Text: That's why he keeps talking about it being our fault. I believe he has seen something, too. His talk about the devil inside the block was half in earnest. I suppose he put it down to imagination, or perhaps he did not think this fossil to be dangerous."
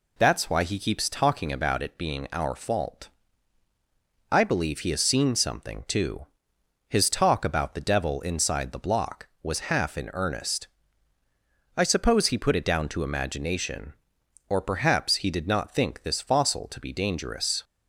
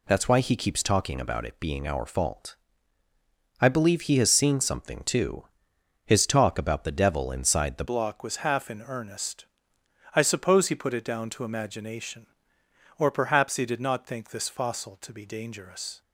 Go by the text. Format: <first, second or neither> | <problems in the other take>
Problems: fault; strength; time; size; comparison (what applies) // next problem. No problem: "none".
first | changes voice at "block"; from 7.8 s on; 8.2 s long